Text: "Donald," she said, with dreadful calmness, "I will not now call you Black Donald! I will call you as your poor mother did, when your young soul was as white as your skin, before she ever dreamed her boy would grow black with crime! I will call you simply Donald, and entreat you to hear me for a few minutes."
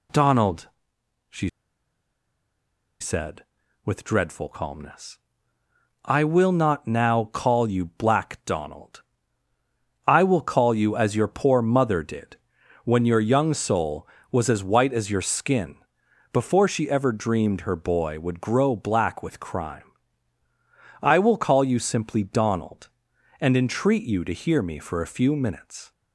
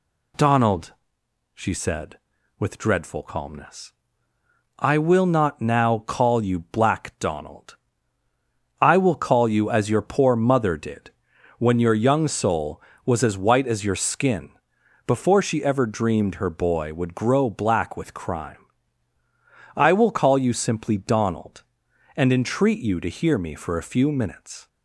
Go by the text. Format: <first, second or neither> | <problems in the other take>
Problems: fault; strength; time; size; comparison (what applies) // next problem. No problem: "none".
second | pauses between "she" and "said"; strong; at 1.4 s; 1.5 s long